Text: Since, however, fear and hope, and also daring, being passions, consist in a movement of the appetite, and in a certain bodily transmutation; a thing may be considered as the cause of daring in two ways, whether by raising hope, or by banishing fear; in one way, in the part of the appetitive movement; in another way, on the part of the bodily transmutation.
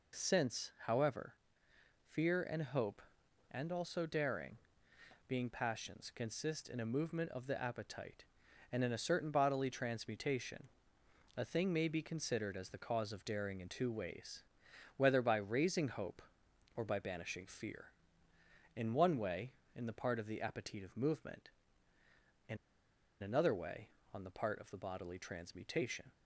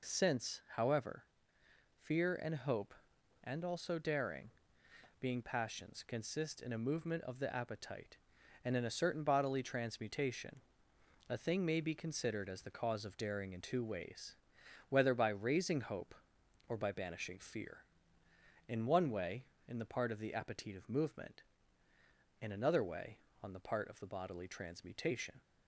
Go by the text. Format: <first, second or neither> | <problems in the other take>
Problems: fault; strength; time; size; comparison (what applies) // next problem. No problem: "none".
second | pauses between "in" and "another"; noticeable; at 22.5 s; 0.66 s long